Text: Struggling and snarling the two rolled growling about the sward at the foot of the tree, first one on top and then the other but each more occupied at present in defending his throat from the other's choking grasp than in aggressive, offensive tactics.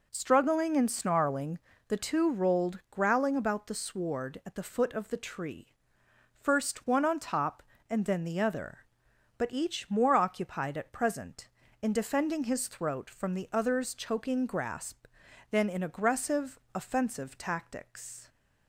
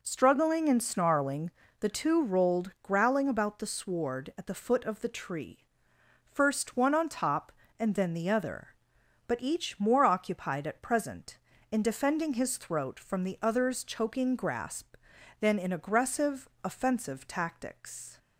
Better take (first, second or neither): neither